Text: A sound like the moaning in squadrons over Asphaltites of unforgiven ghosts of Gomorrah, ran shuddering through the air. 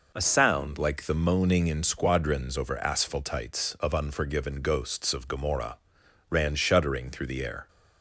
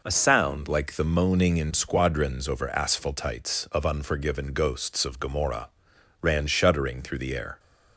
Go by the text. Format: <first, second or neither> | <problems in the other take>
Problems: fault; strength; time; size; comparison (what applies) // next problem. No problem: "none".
neither | none